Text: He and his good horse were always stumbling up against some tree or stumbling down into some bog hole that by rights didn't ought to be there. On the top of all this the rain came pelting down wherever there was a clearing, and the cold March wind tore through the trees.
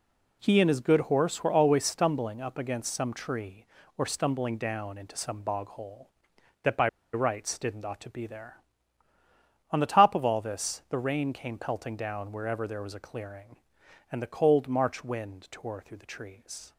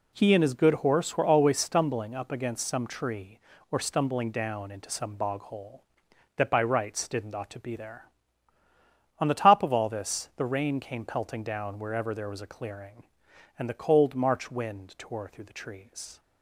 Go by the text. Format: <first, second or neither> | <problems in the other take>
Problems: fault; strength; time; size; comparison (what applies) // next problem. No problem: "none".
second | pauses between "by" and "rights"; slight; at 6.8 s; 0.24 s long